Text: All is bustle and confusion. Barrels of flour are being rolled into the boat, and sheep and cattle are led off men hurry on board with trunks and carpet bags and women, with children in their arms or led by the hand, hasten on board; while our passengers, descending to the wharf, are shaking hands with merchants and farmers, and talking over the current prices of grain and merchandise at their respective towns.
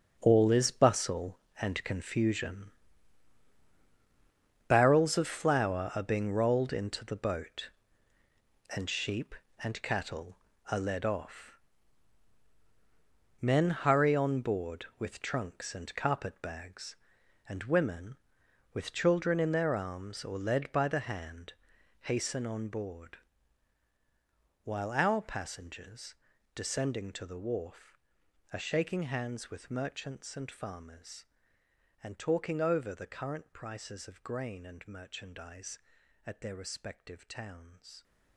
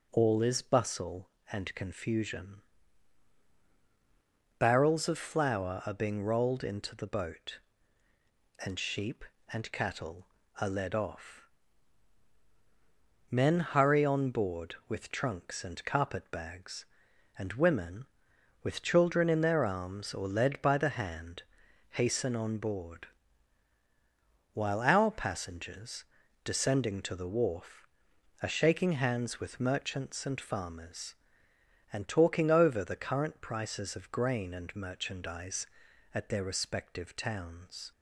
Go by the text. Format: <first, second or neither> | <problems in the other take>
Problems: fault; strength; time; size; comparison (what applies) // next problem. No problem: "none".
second | gets quieter; strong; throughout; 12.5 dB // pauses between "off" and "men"; strong; at 11.5 s; 1.8 s long; strong in the second